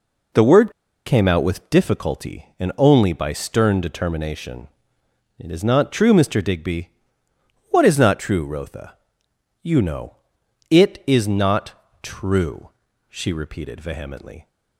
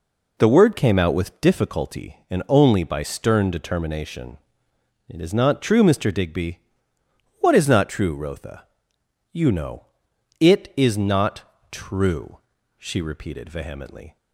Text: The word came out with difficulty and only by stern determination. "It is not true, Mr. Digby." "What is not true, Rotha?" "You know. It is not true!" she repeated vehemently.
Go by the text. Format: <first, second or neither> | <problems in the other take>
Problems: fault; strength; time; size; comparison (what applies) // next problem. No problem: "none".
second | pauses between "word" and "came"; slight; at 0.7 s; 0.34 s long // pauses between "not" and "true"; slight; at 11.7 s; 0.30 s long; slight in the second